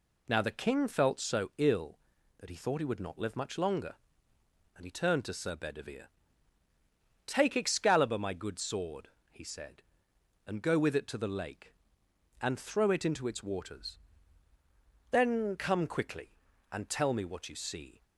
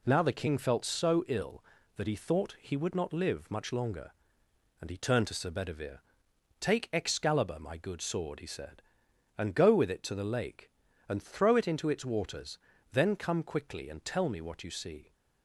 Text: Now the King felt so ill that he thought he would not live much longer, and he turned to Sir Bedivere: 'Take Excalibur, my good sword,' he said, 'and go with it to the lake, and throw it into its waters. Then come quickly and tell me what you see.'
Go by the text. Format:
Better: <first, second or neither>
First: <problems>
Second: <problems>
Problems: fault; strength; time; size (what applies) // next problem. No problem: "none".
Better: neither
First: none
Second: none